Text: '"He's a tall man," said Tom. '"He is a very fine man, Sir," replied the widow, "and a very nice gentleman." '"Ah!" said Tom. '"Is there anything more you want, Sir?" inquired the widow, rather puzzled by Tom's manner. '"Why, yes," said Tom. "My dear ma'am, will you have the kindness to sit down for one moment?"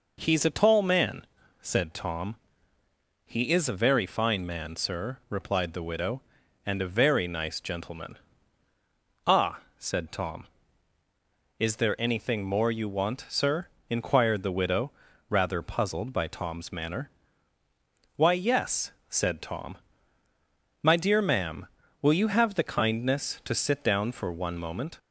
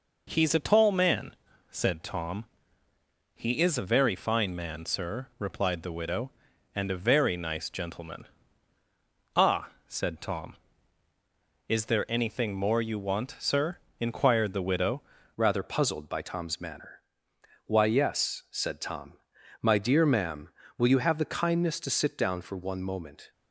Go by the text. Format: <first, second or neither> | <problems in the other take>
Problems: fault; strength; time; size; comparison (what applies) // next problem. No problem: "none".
first | changes voice at "rather"; from 15.3 s on; 8.0 s long